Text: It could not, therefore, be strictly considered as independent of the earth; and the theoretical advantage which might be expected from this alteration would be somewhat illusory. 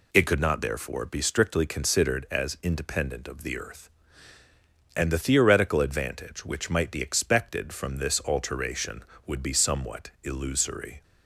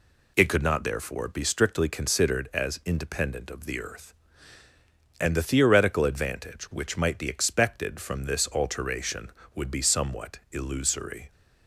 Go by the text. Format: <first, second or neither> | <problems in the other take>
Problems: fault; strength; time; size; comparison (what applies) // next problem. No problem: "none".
neither | none